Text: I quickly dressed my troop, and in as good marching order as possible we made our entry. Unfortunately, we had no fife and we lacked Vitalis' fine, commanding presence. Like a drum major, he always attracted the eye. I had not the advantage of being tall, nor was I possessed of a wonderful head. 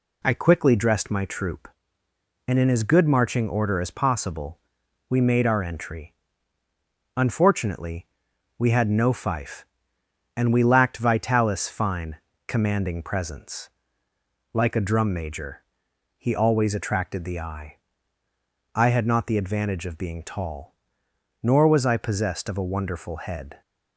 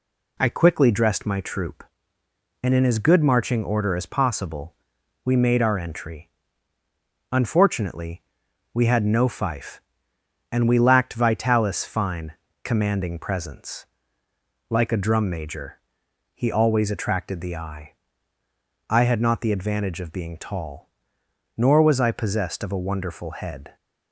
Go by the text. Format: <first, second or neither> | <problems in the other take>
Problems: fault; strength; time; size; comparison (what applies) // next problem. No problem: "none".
neither | pauses between "possible" and "we"; noticeable; the same in both